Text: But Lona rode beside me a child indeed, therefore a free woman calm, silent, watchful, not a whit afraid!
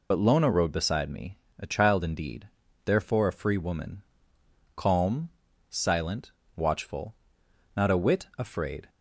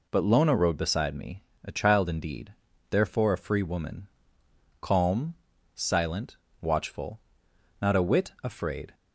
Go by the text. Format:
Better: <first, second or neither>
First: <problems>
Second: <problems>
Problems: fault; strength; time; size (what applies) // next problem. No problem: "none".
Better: second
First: loses the start of "But"; at 0.1 s; 55 ms // pauses between "me" and "a"; slight; at 1.3 s; 0.22 s long // pauses between "woman" and "calm"; noticeable; at 4.0 s; 0.72 s long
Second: pauses between "me" and "a"; slight; at 1.4 s; 0.22 s long // pauses between "woman" and "calm"; noticeable; at 4.0 s; 0.72 s long